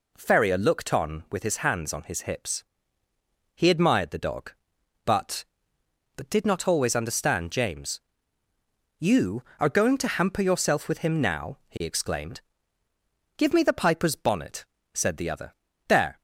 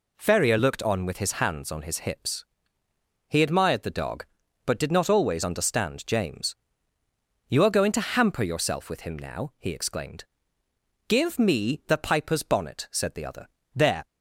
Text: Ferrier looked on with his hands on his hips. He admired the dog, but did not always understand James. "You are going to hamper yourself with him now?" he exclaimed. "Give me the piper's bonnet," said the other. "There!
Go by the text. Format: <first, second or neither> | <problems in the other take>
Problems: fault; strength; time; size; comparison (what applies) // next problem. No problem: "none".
second | says "but" twice; at 6.1 s